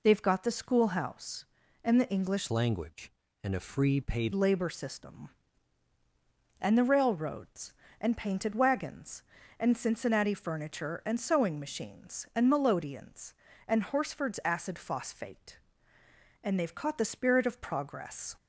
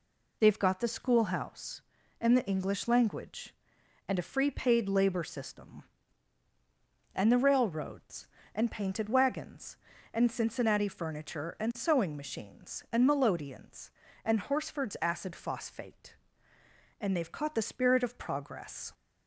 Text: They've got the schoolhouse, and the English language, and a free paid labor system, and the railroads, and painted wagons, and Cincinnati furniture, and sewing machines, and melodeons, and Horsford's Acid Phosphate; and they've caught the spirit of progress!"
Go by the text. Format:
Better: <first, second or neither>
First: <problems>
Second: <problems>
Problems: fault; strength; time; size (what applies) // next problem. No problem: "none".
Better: second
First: changes voice from "language" to "paid"; from 2.5 to 4.3 s; 1.8 s long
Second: none